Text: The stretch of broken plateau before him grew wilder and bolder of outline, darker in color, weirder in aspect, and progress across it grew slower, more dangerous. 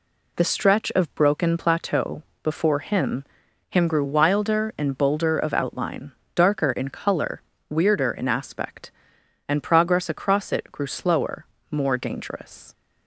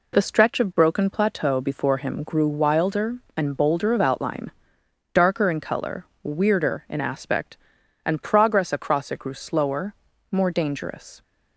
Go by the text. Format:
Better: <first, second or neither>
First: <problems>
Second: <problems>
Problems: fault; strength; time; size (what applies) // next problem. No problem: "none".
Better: second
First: pauses between "plateau" and "before"; slight; at 2.2 s; 0.22 s long // says "him" twice; at 3.6 s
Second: none